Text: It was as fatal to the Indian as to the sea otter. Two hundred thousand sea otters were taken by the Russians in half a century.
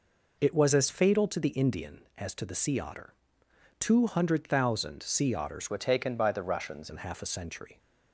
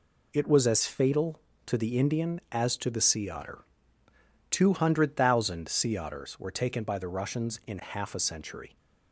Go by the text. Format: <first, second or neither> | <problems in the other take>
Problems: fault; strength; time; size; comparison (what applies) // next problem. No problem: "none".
second | changes voice from "were" to "Russians"; from 5.6 to 6.9 s; 1.3 s long